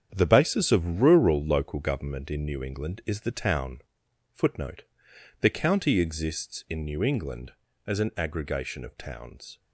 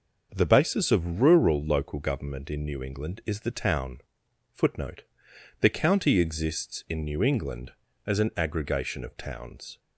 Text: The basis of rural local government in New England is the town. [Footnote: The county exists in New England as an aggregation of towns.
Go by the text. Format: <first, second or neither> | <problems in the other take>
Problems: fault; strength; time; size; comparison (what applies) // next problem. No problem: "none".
second | gets quieter; strong; throughout; 8.5 dB // starts louder than the rest; strong; until 1.1 s; 8 dB; noticeable in the second